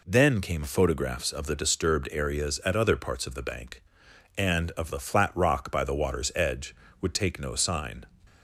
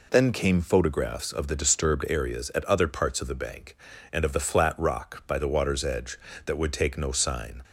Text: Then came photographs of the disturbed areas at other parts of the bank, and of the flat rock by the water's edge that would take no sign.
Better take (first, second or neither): second